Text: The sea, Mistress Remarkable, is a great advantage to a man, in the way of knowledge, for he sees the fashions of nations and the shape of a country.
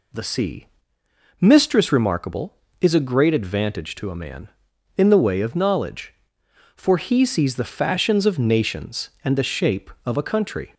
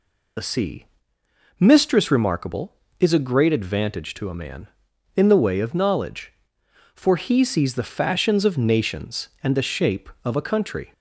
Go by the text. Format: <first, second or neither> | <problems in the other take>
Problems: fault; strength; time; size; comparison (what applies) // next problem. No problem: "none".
first | loses the start of "The"; at 0.3 s; 45 ms